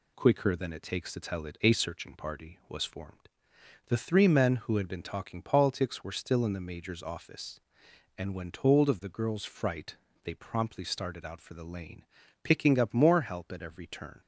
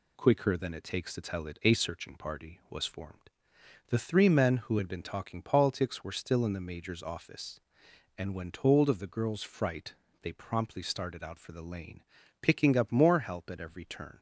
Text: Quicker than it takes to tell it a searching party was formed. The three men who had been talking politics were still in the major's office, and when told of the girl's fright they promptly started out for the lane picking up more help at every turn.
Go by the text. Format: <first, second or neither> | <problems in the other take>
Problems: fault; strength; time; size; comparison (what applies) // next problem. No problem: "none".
neither | pauses between "fright" and "they"; slight; the same in both // pauses between "lane" and "picking"; the same in both